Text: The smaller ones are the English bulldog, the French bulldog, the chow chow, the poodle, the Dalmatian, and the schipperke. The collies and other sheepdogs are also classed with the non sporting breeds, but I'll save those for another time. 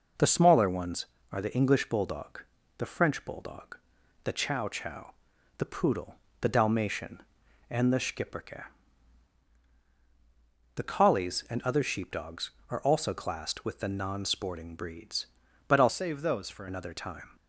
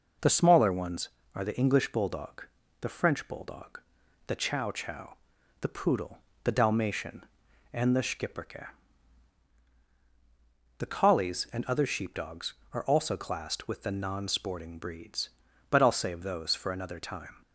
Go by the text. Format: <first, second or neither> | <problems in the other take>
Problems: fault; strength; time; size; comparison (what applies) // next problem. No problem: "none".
second | changes voice from "save" to "for"; from 15.8 to 16.6 s; 0.8 s long